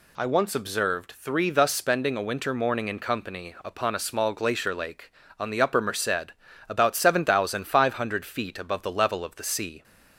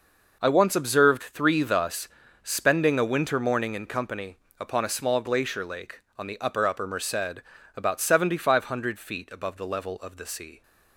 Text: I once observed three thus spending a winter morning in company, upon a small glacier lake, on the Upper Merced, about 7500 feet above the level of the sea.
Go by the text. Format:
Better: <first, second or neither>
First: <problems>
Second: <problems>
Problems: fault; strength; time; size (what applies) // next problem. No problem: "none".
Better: first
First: none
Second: pauses between "thus" and "spending"; at 2.0 s; 0.38 s long // says "Upper" twice; at 6.6 s